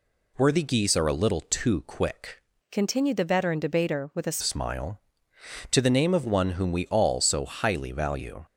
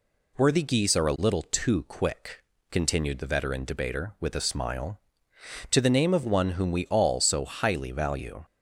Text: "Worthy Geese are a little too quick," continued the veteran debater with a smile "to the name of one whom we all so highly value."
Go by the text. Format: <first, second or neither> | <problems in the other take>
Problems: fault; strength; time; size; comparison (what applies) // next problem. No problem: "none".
second | changes voice from "continued" to "a"; from 2.7 to 4.3 s; 1.6 s long